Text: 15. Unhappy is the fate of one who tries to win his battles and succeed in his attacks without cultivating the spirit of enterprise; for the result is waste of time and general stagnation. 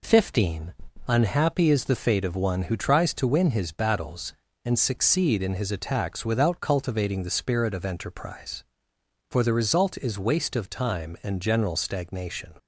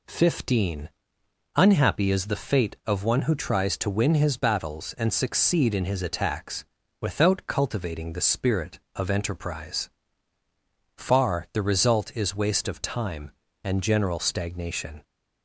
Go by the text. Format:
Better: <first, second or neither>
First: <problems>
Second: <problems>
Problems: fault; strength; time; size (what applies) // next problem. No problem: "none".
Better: first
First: none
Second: pauses between "attacks" and "without"; slight; at 6.6 s; 0.36 s long // says "far" for "for"; at 10.9 s